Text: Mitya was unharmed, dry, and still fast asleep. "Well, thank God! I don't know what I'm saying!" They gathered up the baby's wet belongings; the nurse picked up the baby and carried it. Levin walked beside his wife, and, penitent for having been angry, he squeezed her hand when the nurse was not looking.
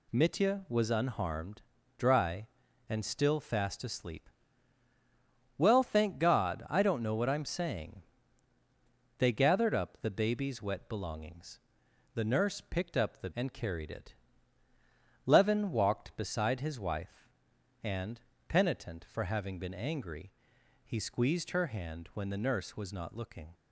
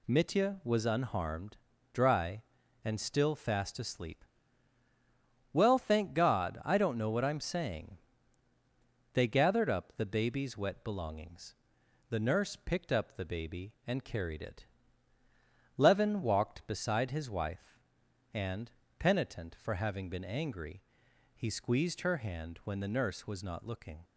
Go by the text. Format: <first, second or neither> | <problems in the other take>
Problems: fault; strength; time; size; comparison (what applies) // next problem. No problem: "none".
second | skips "baby"; at 13.3 s